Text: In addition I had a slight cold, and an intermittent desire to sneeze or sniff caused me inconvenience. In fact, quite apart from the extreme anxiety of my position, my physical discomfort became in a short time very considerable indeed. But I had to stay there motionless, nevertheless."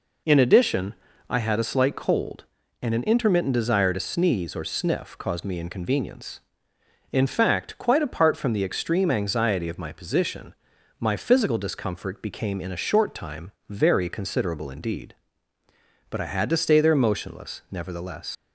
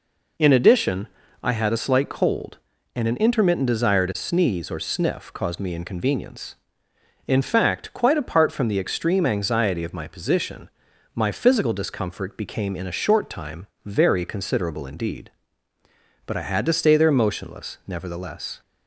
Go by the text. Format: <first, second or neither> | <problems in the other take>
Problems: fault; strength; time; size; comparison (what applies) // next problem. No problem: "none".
second | pauses between "addition" and "I"; slight; at 0.9 s; 0.36 s long; slight in the second // pauses between "time" and "very"; slight; at 13.5 s; 0.17 s long; slight in the second // leaves "nevertheless" unfinished; at 18.3 s; 95 ms